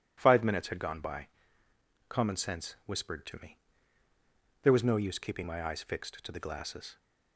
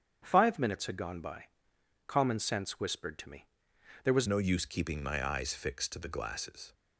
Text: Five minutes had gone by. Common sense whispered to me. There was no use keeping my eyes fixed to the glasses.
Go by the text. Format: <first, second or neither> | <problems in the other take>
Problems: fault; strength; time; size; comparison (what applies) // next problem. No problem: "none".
first | starts louder than the rest; strong; until 1.2 s; 7.5 dB // changes voice at "no"; from 4.2 s on; 2.5 s long